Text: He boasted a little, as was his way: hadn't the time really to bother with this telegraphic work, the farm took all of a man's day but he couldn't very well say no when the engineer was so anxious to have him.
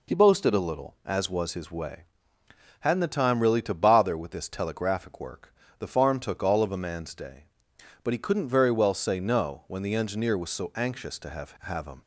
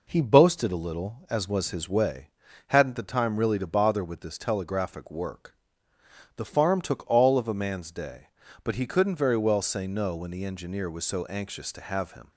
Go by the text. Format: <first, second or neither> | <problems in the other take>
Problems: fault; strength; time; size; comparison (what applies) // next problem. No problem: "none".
second | says "have" twice; at 11.6 s